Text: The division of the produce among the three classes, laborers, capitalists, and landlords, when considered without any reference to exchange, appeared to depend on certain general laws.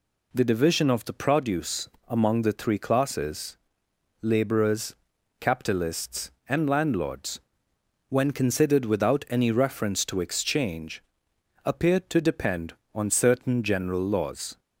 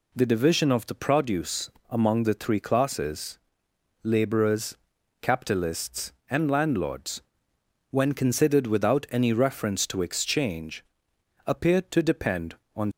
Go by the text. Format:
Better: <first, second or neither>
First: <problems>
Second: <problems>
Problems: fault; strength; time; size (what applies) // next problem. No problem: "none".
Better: first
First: pauses between "produce" and "among"; slight; at 1.8 s; 0.18 s long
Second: pauses between "produce" and "among"; slight; at 1.7 s; 0.18 s long // stops before "certain general laws"; at 12.9 s